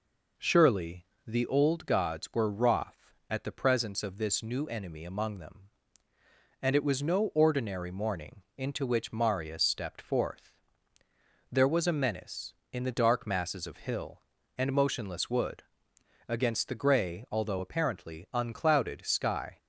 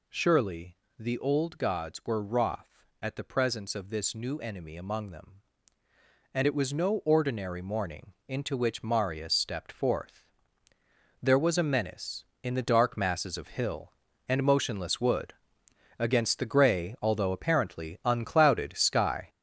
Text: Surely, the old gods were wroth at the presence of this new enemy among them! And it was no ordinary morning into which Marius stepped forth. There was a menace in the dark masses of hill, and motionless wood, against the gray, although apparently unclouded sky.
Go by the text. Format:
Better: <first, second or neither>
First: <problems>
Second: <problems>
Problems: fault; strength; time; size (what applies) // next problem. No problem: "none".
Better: first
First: none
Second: gets louder; strong; throughout; 7.5 dB